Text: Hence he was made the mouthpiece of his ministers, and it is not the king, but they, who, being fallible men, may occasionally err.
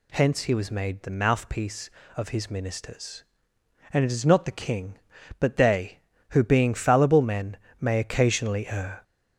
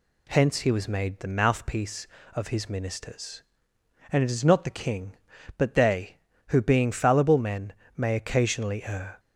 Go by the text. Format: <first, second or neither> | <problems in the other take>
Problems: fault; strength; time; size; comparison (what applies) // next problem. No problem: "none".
second | gets louder; noticeable; throughout; 4 dB